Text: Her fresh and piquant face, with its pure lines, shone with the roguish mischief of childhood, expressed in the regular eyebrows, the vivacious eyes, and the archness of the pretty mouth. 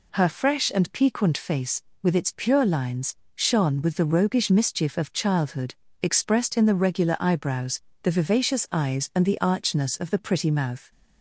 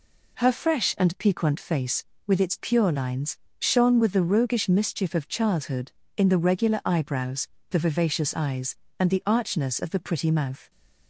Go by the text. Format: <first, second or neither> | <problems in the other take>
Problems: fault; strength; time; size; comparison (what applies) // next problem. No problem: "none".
first | skips "expressed"; at 6.0 s